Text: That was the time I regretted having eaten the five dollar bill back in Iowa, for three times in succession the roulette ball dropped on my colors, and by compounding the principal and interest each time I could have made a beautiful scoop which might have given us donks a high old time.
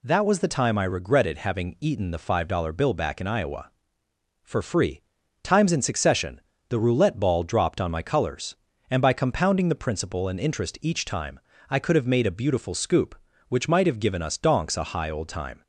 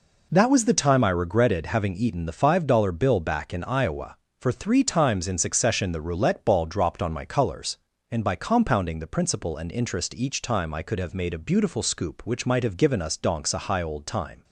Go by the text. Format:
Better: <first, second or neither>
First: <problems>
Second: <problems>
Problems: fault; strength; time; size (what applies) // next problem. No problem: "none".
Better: second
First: says "free" for "three"; at 4.6 s // pauses between "succession" and "the"; slight; at 6.4 s; 0.28 s long // pauses between "time" and "I"; slight; at 11.4 s; 0.30 s long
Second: none